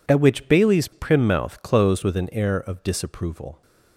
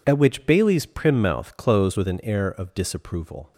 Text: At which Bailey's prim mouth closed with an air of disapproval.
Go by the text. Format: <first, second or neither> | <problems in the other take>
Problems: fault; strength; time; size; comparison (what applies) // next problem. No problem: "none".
neither | none